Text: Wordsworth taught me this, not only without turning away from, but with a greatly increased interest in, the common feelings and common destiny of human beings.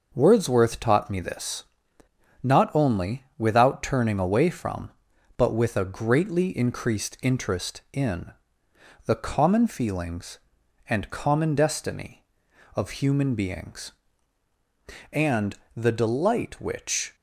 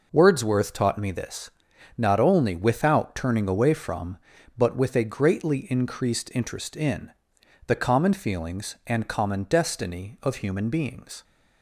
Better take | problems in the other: second | pauses between "only" and "without"; slight; at 3.2 s; 0.16 s long // goes on to say "And the delight which"; strong; from 15.1 s on; 2.0 s long

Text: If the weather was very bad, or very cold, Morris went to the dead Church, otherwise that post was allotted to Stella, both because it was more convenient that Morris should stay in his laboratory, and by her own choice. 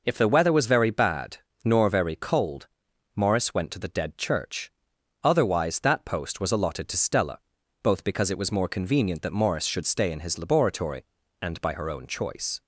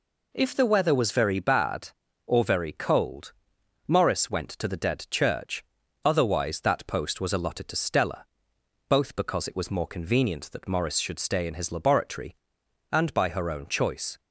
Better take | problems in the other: second | says "nor" for "or"; at 1.6 s

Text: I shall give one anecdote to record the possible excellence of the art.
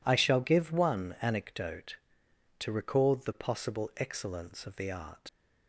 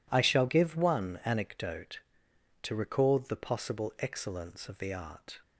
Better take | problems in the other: second | leaves "art" unfinished; at 5.2 s; 100 ms

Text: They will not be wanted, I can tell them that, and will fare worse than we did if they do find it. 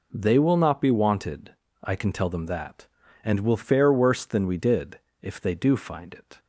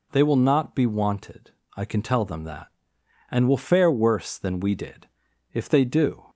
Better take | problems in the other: first | pauses between "did" and "if"; noticeable; at 5.0 s; 0.46 s long; slight in the first // stops before "find it"; at 6.2 s

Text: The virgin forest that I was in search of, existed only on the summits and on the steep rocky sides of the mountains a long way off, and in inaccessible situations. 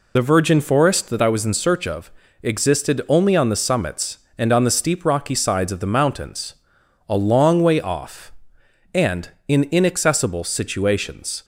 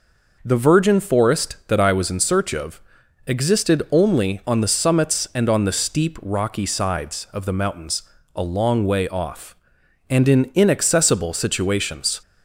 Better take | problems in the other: second | loses the start of "The"; at 0.1 s; 45 ms // pauses between "mountains" and "a"; noticeable; at 6.5 s; 0.56 s long; slight in the second

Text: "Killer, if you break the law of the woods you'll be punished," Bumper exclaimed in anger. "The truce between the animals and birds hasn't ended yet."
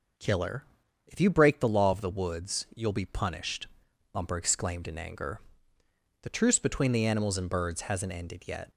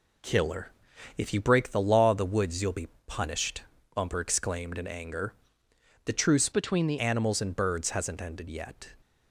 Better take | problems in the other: first | pauses between "be" and "punished"; slight; at 2.8 s; 0.18 s long // changes voice from "between" to "the"; from 6.5 to 6.9 s; 0.4 s long

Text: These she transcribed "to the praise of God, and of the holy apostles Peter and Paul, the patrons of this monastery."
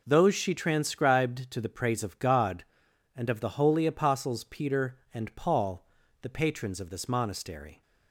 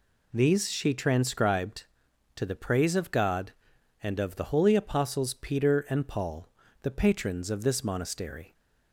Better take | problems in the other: second | says "Those" for "These"; at 0.0 s

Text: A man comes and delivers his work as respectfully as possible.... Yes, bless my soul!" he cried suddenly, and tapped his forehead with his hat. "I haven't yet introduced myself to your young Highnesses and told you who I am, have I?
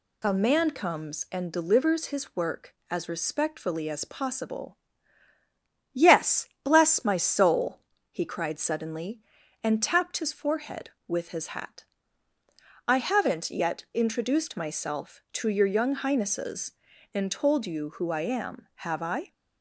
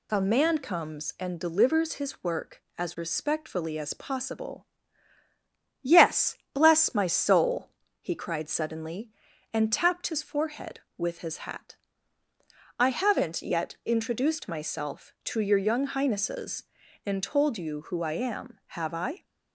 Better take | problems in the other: neither | none

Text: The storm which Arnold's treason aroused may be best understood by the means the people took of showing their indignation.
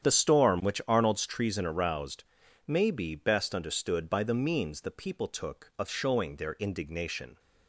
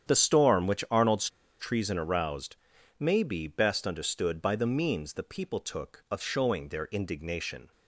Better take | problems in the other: first | starts louder than the rest; strong; until 1.1 s; 9 dB; strong in the first // pauses between "Arnold's" and "treason"; slight; at 1.2 s; 0.31 s long // pauses between "aroused" and "may"; at 2.5 s; 0.42 s long; also in the first

